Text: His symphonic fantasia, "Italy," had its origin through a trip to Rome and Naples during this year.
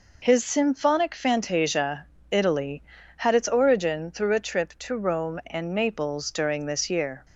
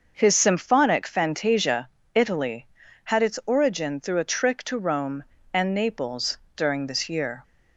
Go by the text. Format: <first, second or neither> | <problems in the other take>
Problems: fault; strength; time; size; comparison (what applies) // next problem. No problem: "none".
first | starts louder than the rest; until 1.1 s; 6 dB // says "trick" for "trip"; at 4.3 s // pauses between "Naples" and "during"; slight; at 6.3 s; 0.18 s long